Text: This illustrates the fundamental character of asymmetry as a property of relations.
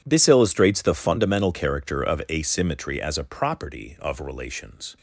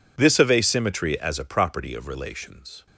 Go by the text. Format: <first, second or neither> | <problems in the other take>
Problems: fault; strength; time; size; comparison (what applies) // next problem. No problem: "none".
first | skips "illustrates the fundamental character"; at 0.3 s